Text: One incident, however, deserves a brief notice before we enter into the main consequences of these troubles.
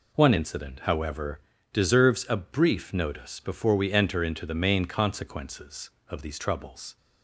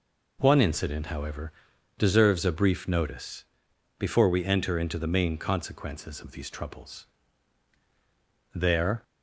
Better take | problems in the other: first | pauses between "notice" and "before"; noticeable; at 3.4 s; 0.54 s long // goes on to say "There"; slight; from 8.5 s on; 0.48 s long

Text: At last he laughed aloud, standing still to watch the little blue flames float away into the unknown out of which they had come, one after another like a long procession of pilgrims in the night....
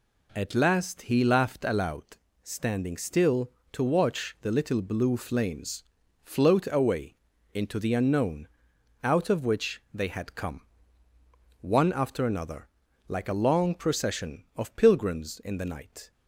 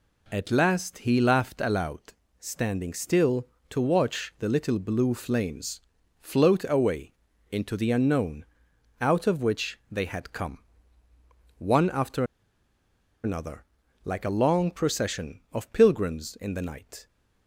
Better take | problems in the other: first | pauses between "flames" and "float"; at 5.7 s; 0.40 s long; also in the first // pauses between "away" and "into"; at 7.1 s; 0.40 s long; also in the first // pauses between "unknown" and "out"; noticeable; at 8.4 s; 0.56 s long; noticeable in the first // pauses between "after" and "another"; at 12.2 s; 0.99 s long // pauses between "another" and "like"; at 13.6 s; 0.40 s long; also in the first

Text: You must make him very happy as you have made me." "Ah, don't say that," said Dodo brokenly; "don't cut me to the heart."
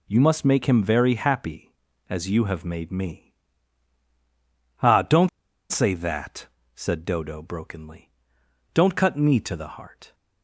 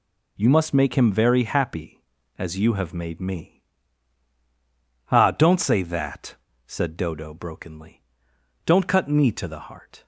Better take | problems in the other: second | pauses between "don't" and "say"; at 5.2 s; 0.40 s long

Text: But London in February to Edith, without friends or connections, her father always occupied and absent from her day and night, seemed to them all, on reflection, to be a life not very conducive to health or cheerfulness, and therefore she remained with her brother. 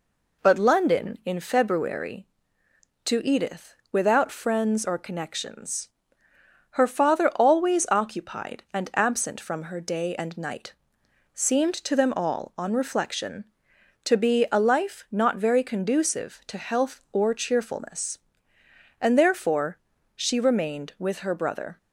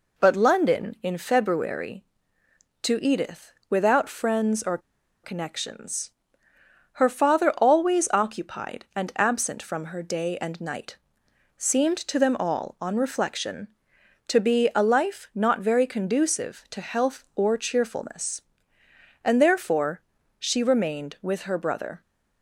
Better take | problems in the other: first | pauses between "or" and "connections"; at 4.7 s; 0.45 s long // pauses between "therefore" and "she"; at 20.0 s; 0.38 s long; also in the first

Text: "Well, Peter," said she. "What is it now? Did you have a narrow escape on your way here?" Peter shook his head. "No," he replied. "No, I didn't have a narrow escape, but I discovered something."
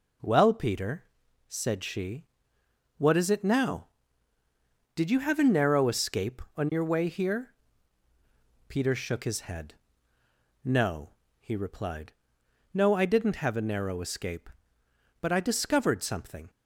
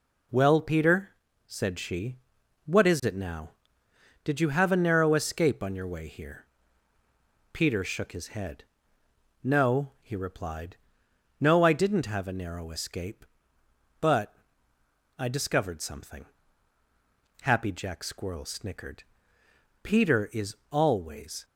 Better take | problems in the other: first | pauses between "but" and "I"; noticeable; at 14.3 s; 0.84 s long // goes on to say "Happy Jack Squirrel snickered Peter is always"; strong; from 17.4 s on; 4.0 s long

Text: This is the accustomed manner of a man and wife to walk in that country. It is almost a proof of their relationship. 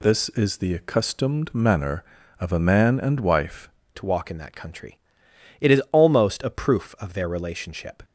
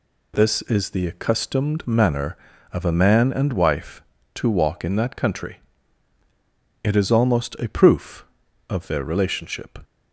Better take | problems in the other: second | changes voice at "to"; from 3.9 s on; 4.1 s long

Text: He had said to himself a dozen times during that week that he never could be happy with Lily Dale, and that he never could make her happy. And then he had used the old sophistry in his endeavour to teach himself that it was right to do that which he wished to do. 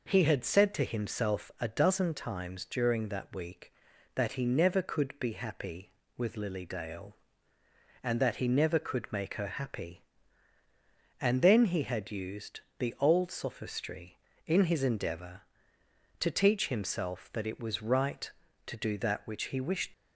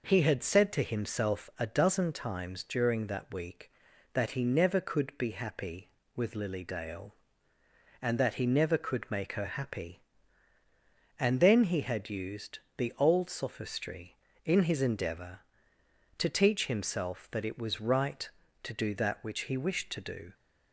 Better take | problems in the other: second | pauses between "used" and "the"; slight; at 12.6 s; 0.18 s long; slight in the second // stops before "to do"; at 19.9 s

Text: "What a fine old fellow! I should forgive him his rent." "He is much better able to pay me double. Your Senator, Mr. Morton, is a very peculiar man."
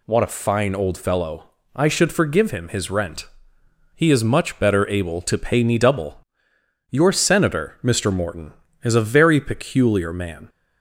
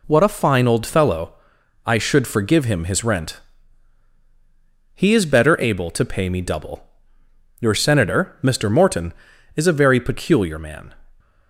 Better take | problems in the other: first | skips "much"; at 5.2 s

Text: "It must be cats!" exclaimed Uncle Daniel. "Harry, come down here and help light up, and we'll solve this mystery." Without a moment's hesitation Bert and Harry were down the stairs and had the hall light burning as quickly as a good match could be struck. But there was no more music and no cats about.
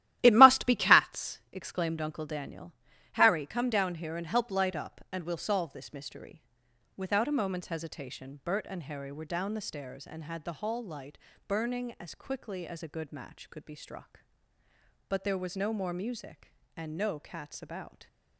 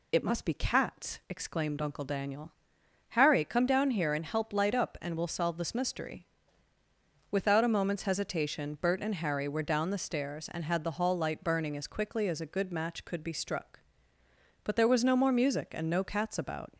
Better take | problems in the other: second | starts louder than the rest; strong; until 1.2 s; 13.5 dB // pauses between "light" and "burning"; slight; at 11.1 s; 0.30 s long

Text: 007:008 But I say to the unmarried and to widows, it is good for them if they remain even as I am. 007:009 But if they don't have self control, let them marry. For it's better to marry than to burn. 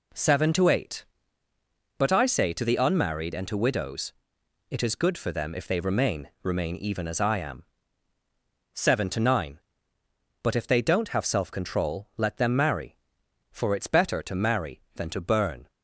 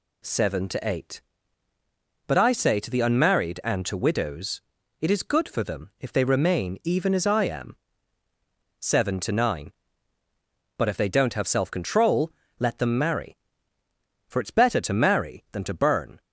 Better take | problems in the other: second | says "remain" twice; at 6.4 s

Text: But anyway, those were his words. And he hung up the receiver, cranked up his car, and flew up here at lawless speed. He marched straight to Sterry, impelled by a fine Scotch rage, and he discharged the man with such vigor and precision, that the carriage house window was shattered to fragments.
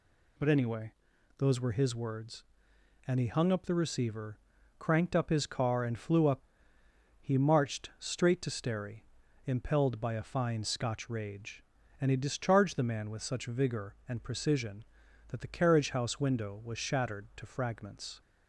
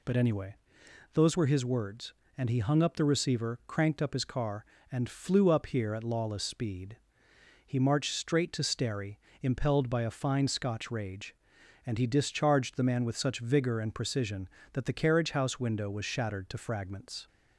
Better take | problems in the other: second | skips "here at lawless speed"; at 6.7 s

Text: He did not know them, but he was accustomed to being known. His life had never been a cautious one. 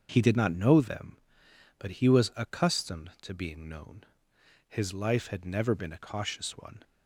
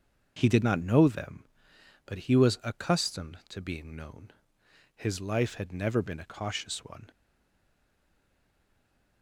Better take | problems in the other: first | starts louder than the rest; until 1.3 s; 6.5 dB; also in the first // stays silent after the last word; noticeable; from 7.1 s on; 2.1 s long

